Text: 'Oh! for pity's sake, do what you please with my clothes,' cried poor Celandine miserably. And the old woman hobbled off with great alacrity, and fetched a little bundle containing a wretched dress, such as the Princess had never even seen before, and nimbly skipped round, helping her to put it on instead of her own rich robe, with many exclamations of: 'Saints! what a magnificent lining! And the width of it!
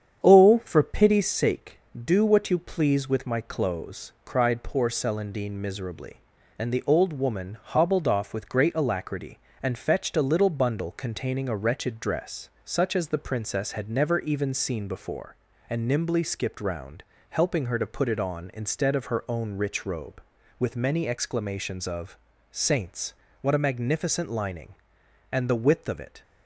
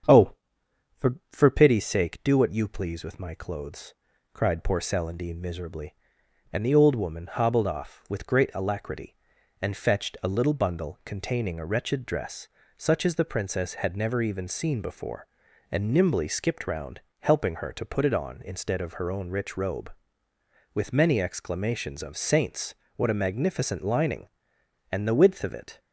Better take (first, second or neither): first